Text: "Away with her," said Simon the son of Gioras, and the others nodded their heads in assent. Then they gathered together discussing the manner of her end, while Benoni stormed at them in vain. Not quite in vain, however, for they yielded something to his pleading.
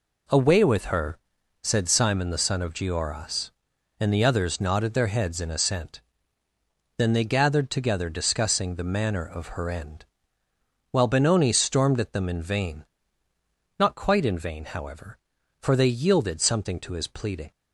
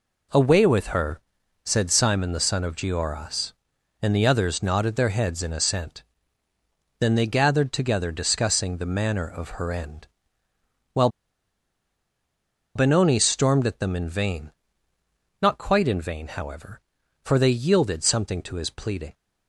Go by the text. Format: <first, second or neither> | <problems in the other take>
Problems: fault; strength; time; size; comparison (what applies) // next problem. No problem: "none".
first | pauses between "while" and "Benoni"; strong; at 11.0 s; 1.6 s long